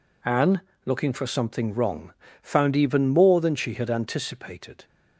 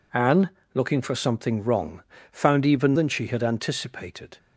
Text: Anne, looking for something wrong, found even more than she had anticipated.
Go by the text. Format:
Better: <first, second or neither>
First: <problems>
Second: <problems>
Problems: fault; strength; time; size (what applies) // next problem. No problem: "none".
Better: first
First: none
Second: skips "more"; at 2.9 s